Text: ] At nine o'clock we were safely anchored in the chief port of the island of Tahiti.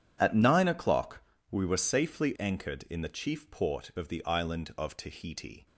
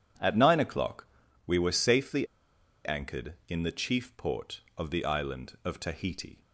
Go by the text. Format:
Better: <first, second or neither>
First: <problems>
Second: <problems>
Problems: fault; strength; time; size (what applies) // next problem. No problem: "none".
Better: first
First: pauses between "o'clock" and "we"; slight; at 1.2 s; 0.28 s long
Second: pauses between "o'clock" and "we"; at 1.0 s; 0.38 s long // pauses between "safely" and "anchored"; noticeable; at 2.2 s; 0.60 s long